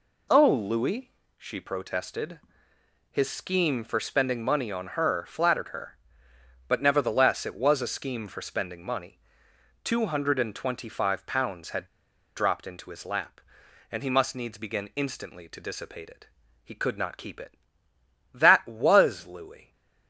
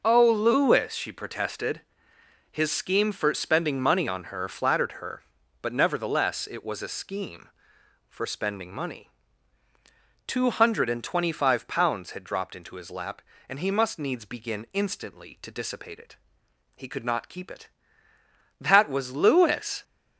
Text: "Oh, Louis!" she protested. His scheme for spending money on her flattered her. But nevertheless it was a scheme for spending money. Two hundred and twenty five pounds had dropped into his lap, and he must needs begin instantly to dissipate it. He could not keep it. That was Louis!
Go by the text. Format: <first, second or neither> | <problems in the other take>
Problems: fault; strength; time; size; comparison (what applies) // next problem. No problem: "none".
second | pauses between "had" and "dropped"; noticeable; at 11.8 s; 0.49 s long